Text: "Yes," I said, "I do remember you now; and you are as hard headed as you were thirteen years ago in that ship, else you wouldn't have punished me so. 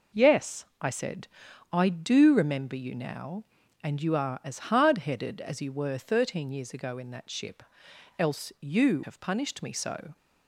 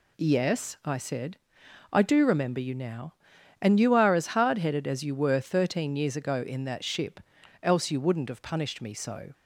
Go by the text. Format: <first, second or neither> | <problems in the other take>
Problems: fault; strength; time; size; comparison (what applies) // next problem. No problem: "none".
second | skips "wouldn't"; at 9.0 s